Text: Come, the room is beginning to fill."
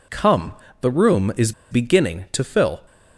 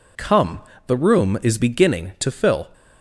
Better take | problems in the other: second | pauses between "is" and "beginning"; slight; at 1.5 s; 0.18 s long

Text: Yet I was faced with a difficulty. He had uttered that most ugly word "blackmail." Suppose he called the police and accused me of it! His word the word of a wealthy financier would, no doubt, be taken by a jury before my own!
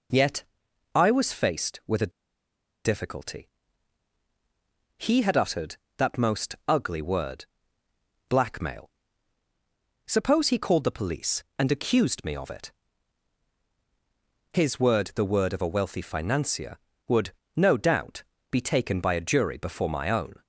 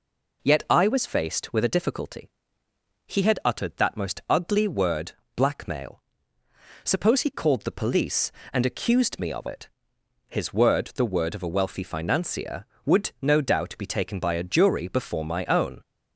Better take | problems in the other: second | pauses between "Yet" and "I"; noticeable; at 0.4 s; 0.50 s long // pauses between "a" and "difficulty"; noticeable; at 2.1 s; 0.74 s long // pauses between "word" and "blackmail"; noticeable; at 7.4 s; 0.82 s long; slight in the second

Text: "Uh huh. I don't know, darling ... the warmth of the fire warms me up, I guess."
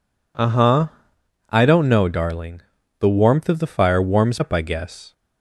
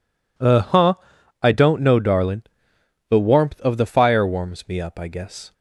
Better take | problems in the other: second | skips "me"; at 4.4 s

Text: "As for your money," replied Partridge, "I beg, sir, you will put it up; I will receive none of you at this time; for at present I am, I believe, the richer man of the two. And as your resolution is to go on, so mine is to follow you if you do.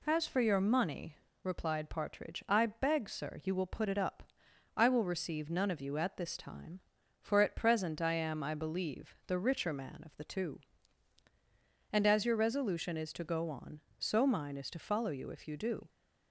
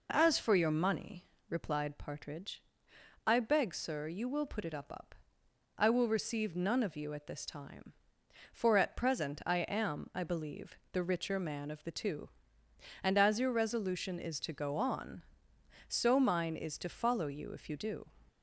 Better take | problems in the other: first | says "up" twice; at 4.9 s

